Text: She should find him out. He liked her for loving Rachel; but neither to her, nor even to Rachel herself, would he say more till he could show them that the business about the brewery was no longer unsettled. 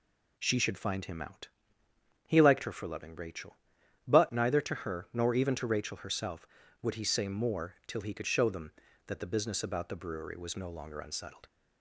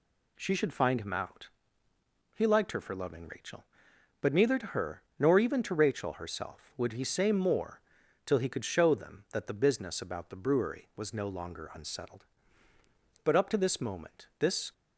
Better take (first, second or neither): first